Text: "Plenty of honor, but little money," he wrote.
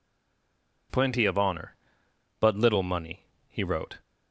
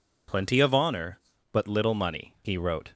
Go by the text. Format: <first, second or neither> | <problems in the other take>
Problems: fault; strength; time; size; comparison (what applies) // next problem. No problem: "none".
second | stays silent before the first word; slight; until 0.8 s; 0.8 s long